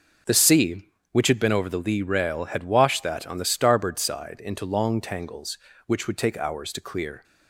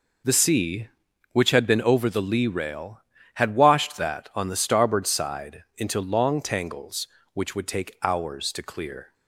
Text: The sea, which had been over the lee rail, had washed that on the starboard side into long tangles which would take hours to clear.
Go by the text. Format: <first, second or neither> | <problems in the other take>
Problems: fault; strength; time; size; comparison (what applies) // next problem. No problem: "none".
neither | none